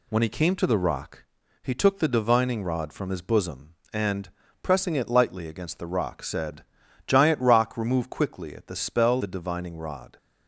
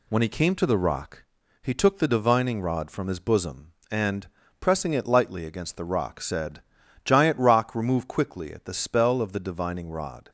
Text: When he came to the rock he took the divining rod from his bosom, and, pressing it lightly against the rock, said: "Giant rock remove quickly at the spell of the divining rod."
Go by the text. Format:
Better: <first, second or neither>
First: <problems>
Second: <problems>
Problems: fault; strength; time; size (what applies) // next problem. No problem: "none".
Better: second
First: pauses between "rock" and "he"; slight; at 1.2 s; 0.36 s long // skips "of"; at 9.2 s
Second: pauses between "rock" and "he"; slight; at 1.2 s; 0.36 s long